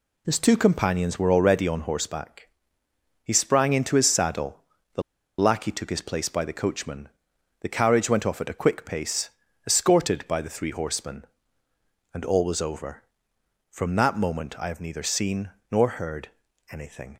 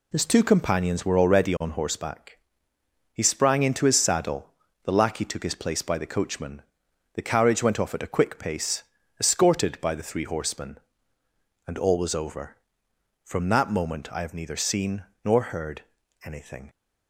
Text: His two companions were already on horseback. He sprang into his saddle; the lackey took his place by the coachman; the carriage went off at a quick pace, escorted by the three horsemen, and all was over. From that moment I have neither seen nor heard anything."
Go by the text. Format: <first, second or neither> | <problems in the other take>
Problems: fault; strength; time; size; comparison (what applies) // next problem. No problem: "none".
second | pauses between "the" and "lackey"; at 5.0 s; 0.36 s long // pauses between "seen" and "nor"; slight; at 15.5 s; 0.22 s long; slight in the second // pauses between "heard" and "anything"; at 16.2 s; 0.42 s long; also in the second